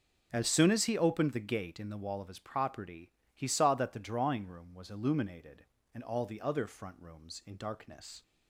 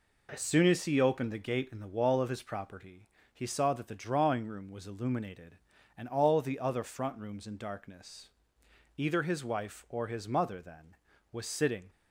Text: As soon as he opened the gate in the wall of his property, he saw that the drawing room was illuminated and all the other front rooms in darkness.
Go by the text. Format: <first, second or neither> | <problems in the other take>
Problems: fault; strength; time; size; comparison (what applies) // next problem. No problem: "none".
first | goes on to say "Either his wife or his mother then was sitting"; strong; from 8.9 s on; 2.9 s long